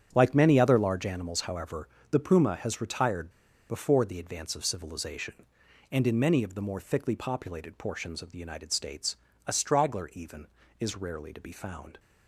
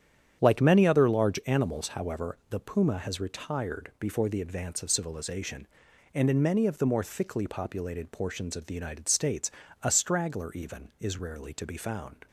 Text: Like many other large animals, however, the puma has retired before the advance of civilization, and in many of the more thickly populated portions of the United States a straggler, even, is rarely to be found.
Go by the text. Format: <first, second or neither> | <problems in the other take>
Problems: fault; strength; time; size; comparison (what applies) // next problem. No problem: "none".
second | starts louder than the rest; strong; until 1.1 s; 8.5 dB; strong in the second // pauses between "retired" and "before"; at 3.2 s; 0.40 s long // pauses between "States" and "a"; slight; at 9.1 s; 0.30 s long; slight in the second